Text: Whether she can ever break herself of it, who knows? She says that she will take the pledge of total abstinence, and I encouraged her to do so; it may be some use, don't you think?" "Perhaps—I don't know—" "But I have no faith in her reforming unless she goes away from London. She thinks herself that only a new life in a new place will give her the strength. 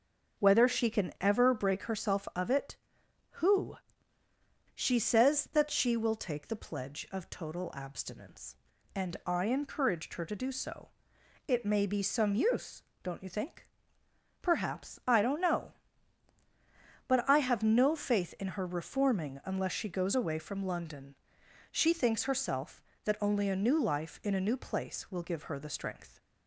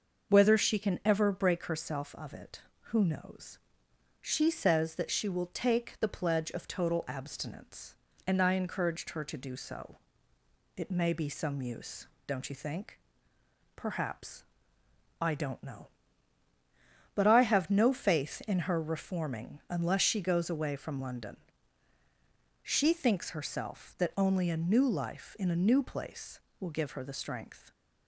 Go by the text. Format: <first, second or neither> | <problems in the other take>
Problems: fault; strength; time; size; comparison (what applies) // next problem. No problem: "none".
second | starts louder than the rest; until 1.4 s; 6 dB; noticeable in the second // skips "knows"; at 4.2 s